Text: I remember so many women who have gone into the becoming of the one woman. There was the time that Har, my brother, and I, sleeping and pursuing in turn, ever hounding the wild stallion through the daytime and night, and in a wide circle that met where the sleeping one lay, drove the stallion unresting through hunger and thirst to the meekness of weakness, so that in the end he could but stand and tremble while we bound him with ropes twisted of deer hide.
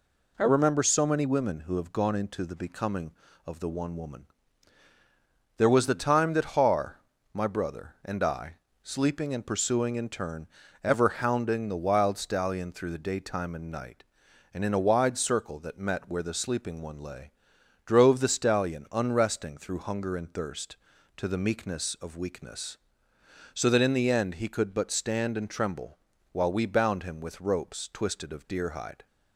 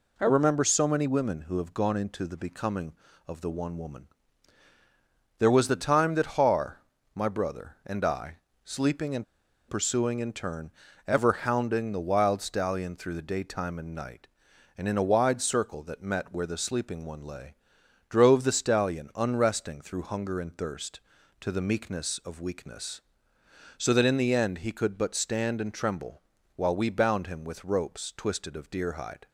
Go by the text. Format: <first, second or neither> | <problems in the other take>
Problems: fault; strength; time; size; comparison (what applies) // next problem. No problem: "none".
first | pauses between "and" and "pursuing"; at 9.2 s; 0.45 s long // pauses between "tremble" and "while"; slight; at 26.2 s; 0.34 s long; slight in the first